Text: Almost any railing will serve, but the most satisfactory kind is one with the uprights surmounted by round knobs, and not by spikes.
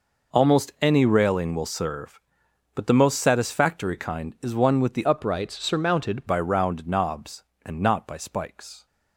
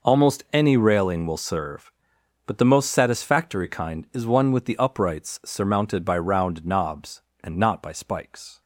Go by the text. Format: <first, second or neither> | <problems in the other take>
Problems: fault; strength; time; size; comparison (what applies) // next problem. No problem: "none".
second | changes voice from "uprights" to "surmounted"; from 5.0 to 6.2 s; 1.2 s long